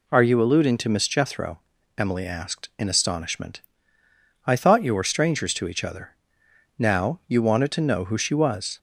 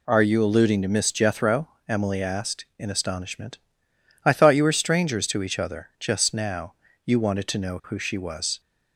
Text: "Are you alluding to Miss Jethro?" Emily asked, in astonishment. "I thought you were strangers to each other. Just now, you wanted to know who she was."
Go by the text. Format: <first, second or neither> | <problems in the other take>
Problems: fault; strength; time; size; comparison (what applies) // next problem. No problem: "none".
second | skips "Just"; at 6.4 s